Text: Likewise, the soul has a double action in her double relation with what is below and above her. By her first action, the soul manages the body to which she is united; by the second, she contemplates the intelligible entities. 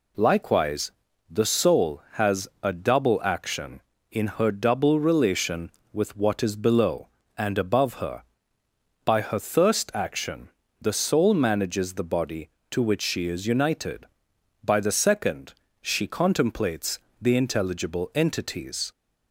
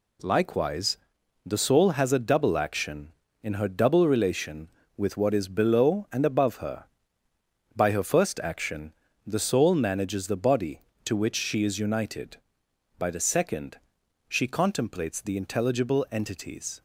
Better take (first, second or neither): second